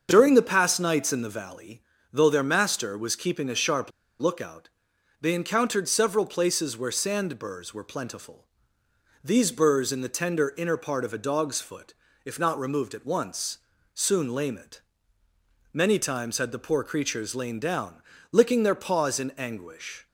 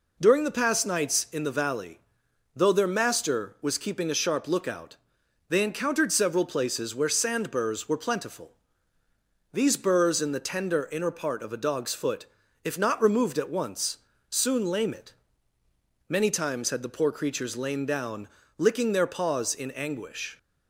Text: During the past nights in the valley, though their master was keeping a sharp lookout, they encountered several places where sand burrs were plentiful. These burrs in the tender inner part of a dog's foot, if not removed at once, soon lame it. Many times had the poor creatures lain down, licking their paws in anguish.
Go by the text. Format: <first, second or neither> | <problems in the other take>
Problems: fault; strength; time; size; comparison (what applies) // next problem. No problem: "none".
second | starts louder than the rest; until 1.1 s; 7 dB // pauses between "sharp" and "lookout"; slight; at 3.9 s; 0.29 s long